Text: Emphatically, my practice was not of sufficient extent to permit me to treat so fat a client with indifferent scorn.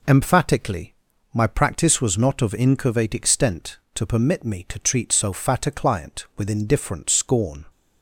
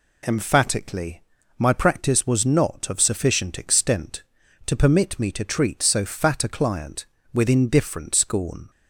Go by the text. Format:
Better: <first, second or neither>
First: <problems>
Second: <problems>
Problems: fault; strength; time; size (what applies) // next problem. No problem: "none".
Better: second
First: says "incurvate" for "sufficient"; at 2.5 s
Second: none